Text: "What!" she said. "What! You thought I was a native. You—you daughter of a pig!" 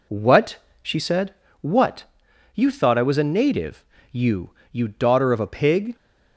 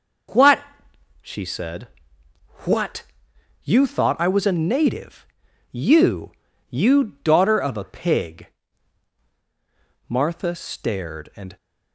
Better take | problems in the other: first | goes on to say "Martha stared and"; from 10.0 s on; 1.5 s long

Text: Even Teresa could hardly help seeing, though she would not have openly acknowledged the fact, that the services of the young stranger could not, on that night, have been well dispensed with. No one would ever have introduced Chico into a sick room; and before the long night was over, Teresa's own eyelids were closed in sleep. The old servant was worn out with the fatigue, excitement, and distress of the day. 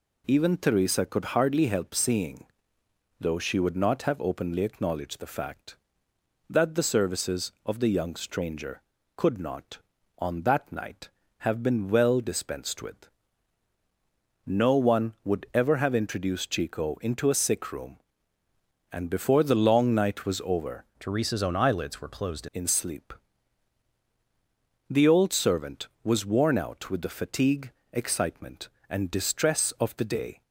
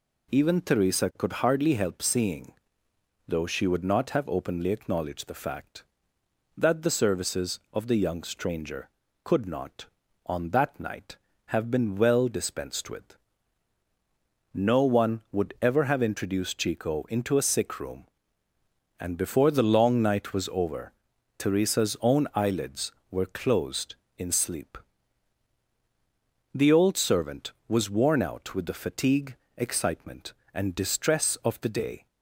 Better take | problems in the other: second | changes voice from "Teresa's" to "closed"; from 21.0 to 22.4 s; 1.4 s long

